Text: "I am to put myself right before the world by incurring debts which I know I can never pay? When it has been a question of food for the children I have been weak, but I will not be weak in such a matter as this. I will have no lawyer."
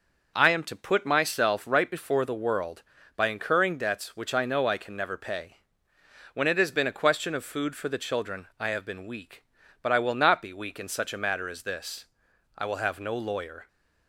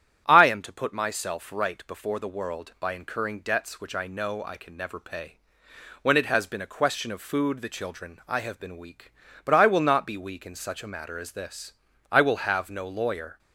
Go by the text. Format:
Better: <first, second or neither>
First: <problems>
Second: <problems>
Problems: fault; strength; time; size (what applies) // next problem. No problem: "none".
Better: first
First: none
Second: starts louder than the rest; strong; until 1.2 s; 10 dB // skips "for"; at 7.6 s